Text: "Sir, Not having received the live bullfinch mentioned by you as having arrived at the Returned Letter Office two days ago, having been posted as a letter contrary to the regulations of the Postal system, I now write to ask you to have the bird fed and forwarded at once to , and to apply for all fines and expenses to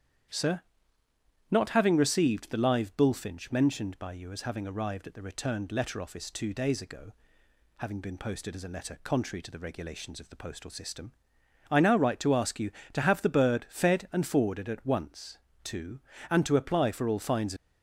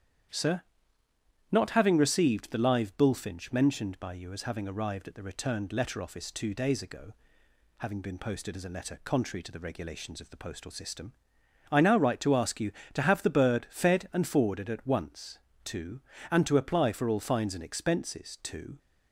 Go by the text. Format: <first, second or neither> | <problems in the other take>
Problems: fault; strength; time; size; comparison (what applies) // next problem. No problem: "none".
second | starts louder than the rest; strong; until 2.1 s; 9.5 dB; strong in the second // stops before "and expenses to"; at 17.5 s